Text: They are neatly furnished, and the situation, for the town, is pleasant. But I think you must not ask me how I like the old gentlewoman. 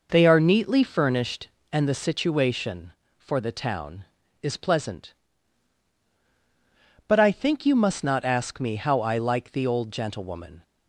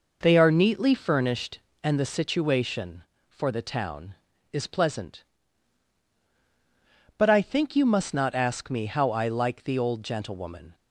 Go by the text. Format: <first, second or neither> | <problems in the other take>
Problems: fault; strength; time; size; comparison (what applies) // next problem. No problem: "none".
neither | none